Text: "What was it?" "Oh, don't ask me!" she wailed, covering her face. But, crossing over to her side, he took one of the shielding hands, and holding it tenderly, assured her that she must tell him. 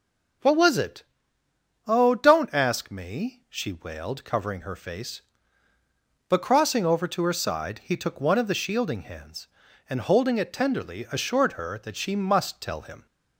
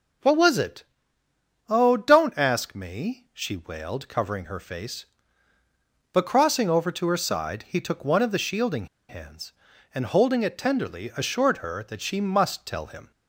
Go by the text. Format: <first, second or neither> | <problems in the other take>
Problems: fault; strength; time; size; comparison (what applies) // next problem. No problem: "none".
first | pauses between "shielding" and "hands"; slight; at 8.8 s; 0.23 s long